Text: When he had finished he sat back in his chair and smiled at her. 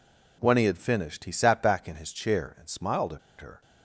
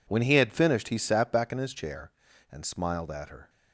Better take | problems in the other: second | pauses between "at" and "her"; slight; at 3.1 s; 0.21 s long

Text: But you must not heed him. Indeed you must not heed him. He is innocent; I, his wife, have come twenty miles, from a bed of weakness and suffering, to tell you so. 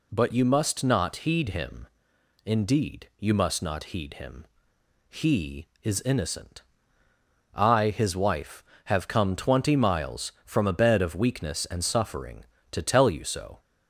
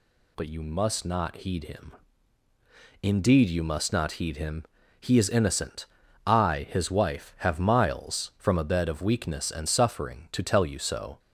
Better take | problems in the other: first | skips "come twenty"; at 7.5 s

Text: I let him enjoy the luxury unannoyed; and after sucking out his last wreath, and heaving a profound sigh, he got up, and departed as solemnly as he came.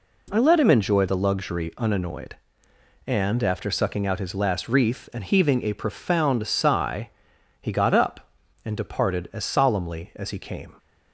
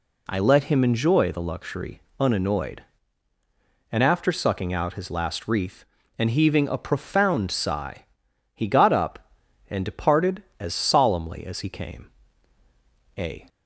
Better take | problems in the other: first | pauses between "luxury" and "unannoyed"; slight; at 2.0 s; 0.18 s long // goes on to say "A"; slight; from 13.1 s on; 0.28 s long

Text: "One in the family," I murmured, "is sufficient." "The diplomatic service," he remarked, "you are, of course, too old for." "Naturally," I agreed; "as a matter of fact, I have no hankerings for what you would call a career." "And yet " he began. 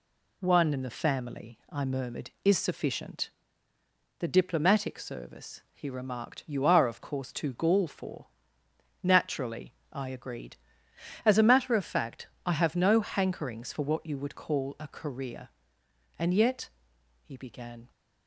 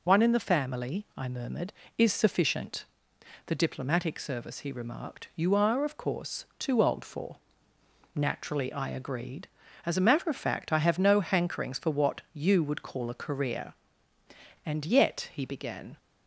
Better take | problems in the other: second | says "gall" for "old"; at 7.5 s

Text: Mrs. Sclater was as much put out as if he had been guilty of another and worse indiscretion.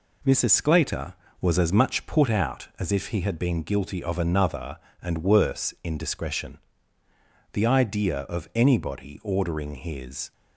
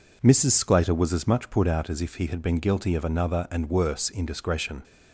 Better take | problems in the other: second | goes on to say "The idea of anybody ordering his"; strong; from 7.5 s on; 2.7 s long

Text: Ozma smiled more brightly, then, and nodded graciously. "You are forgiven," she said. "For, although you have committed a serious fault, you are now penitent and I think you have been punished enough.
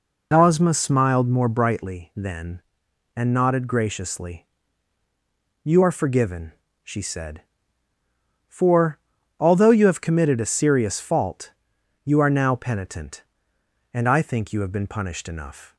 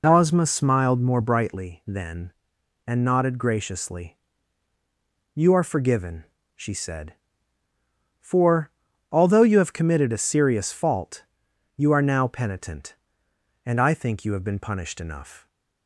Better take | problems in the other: neither | none

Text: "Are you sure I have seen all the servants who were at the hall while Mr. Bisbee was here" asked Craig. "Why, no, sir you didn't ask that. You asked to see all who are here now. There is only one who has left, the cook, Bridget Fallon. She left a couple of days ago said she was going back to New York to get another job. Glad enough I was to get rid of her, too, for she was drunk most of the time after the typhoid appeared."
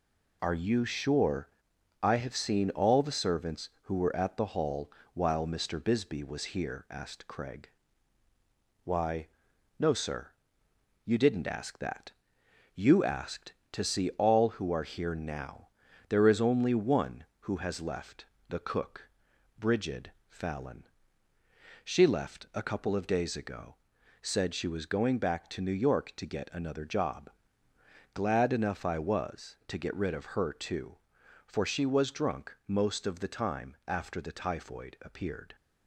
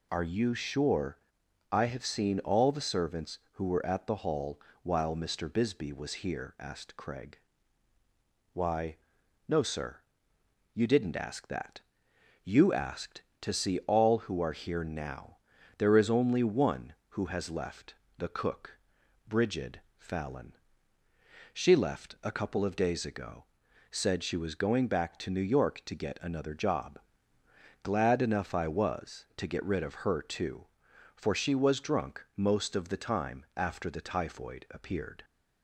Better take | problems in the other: second | gets quieter; noticeable; throughout; 4.5 dB // pauses between "sure" and "I"; noticeable; at 1.4 s; 0.52 s long; noticeable in the second // pauses between "hall" and "while"; slight; at 4.8 s; 0.24 s long; slight in the second // pauses between "sir" and "you"; noticeable; at 10.3 s; 0.74 s long; noticeable in the second // pauses between "Bridget" and "Fallon"; slight; at 20.1 s; 0.18 s long; slight in the second // pauses between "ago" and "said"; noticeable; at 23.7 s; 0.46 s long; noticeable in the second

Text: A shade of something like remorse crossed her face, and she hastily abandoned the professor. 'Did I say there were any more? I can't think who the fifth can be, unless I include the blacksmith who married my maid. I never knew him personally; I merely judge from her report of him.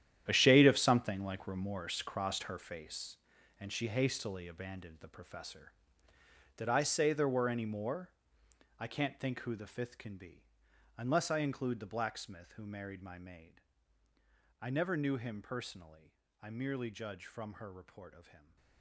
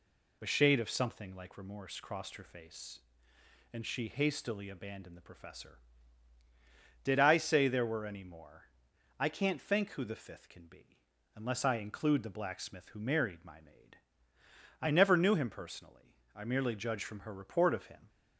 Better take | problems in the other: second | gets quieter; strong; throughout; 14 dB

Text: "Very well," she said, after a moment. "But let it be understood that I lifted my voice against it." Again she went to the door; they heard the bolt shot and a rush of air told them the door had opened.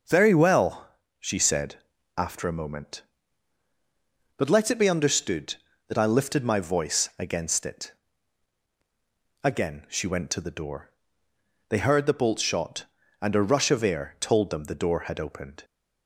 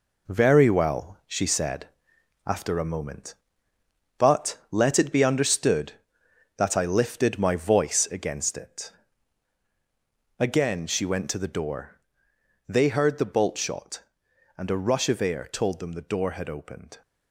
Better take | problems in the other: first | gets quieter; strong; throughout; 7 dB

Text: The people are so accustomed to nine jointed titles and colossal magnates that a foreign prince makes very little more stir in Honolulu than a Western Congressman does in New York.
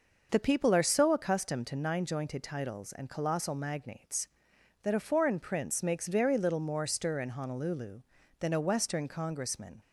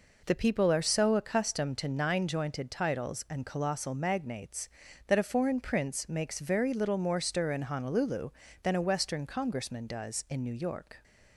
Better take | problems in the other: second | stops before "does in New York"; at 9.8 s

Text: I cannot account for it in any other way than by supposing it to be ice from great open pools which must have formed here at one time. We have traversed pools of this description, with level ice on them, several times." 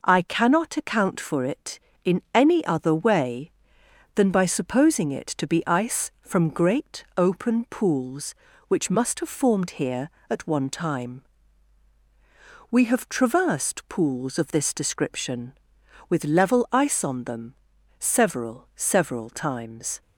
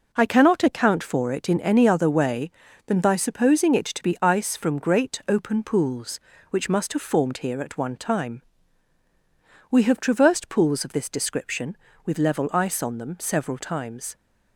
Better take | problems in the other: second | says "several" twice; at 18.7 s

